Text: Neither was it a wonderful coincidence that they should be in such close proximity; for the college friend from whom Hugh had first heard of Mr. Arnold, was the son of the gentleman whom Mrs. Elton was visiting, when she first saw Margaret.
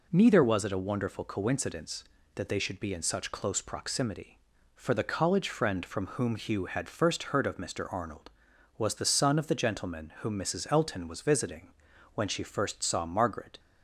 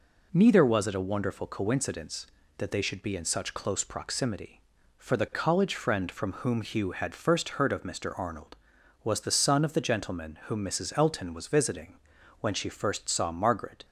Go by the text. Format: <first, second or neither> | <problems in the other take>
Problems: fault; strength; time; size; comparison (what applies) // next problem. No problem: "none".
neither | none